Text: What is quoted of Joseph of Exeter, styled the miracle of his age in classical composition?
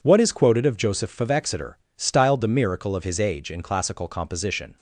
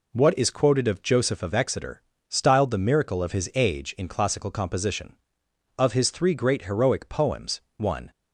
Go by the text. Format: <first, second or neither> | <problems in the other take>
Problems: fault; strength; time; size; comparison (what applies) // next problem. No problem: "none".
first | goes on to say "Of his three great heroic poems one"; strong; from 5.7 s on; 2.3 s long